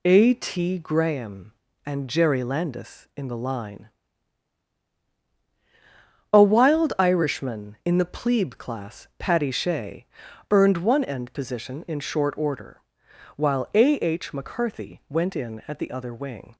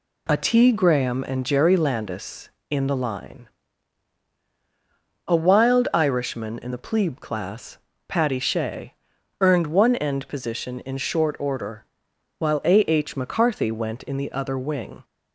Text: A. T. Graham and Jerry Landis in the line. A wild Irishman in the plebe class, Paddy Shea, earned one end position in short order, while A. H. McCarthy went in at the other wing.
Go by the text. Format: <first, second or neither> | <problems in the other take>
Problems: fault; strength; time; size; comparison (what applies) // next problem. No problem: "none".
first | skips "at"; at 14.1 s